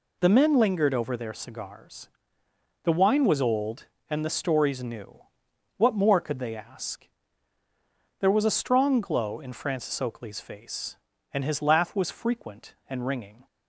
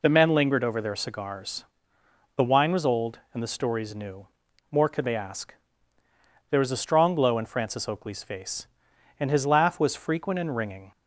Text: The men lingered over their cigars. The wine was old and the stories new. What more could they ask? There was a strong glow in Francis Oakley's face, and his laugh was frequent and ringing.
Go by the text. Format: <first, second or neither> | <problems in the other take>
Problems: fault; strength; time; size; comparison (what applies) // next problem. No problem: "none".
first | skips "What"; at 4.4 s